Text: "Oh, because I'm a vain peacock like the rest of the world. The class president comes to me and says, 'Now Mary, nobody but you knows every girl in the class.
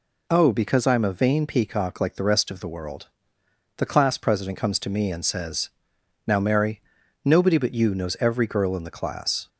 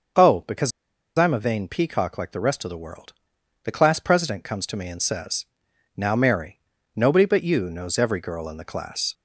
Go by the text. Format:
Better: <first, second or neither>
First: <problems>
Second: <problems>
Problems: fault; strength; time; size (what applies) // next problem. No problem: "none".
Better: first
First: none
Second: starts louder than the rest; until 1.6 s; 6 dB // pauses between "because" and "I'm"; noticeable; at 0.7 s; 0.48 s long